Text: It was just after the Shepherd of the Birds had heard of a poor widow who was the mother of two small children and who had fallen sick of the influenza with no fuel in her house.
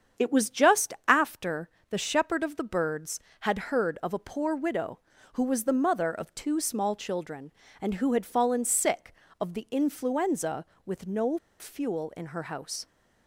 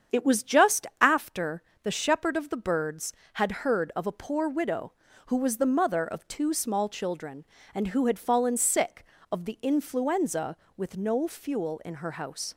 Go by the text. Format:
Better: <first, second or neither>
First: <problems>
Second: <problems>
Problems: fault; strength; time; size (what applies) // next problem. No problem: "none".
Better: second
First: starts louder than the rest; strong; until 1.3 s; 7.5 dB // pauses between "after" and "the"; slight; at 1.6 s; 0.22 s long // pauses between "no" and "fuel"; slight; at 11.3 s; 0.23 s long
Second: starts louder than the rest; strong; until 1.2 s; 7.5 dB // pauses between "after" and "the"; slight; at 1.6 s; 0.22 s long